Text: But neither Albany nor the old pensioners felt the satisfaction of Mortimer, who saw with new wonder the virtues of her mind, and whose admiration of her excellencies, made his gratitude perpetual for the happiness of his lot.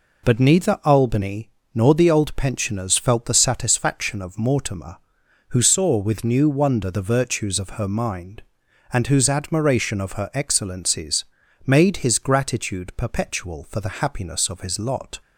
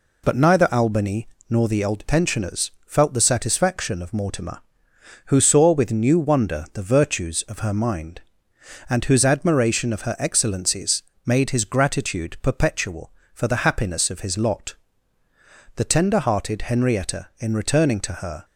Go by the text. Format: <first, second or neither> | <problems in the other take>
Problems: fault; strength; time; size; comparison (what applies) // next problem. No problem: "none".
first | pauses between "Albany" and "nor"; slight; at 1.2 s; 0.20 s long; slight in the first // pauses between "pensioners" and "felt"; slight; at 2.7 s; 0.16 s long // goes on to say "The tender hearted Henrietta in returning to her"; strong; from 15.7 s on; 2.6 s long